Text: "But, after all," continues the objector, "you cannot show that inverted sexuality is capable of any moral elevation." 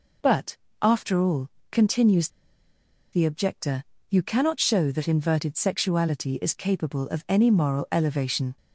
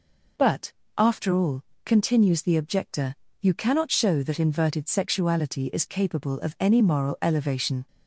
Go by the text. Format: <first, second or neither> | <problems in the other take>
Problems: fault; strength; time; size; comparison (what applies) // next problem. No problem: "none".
second | pauses between "continues" and "the"; noticeable; at 2.2 s; 0.84 s long